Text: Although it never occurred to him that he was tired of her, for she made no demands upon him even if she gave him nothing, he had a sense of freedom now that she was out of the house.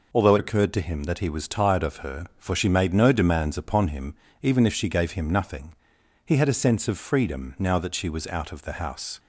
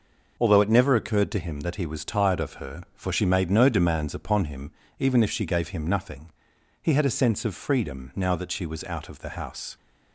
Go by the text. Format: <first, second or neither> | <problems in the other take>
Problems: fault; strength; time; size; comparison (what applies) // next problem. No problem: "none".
second | skips "never"; at 0.3 s // pauses between "him" and "even"; slight; at 4.1 s; 0.26 s long; slight in the second